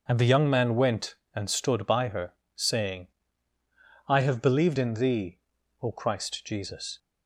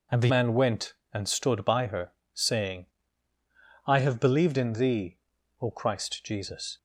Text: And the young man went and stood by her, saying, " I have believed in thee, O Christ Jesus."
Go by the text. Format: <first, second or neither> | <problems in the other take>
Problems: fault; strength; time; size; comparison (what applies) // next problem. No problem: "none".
first | skips "young"; at 0.2 s